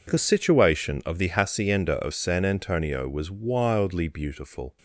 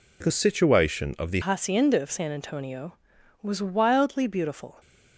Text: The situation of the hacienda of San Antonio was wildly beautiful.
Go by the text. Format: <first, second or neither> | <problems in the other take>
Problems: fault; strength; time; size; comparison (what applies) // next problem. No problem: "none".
first | changes voice at "hacienda"; from 1.4 s on; 3.3 s long